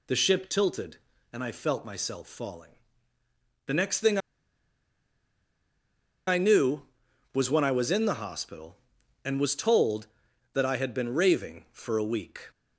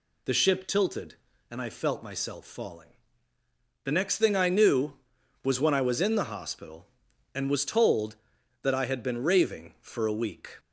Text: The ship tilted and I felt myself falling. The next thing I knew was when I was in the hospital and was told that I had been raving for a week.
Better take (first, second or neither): second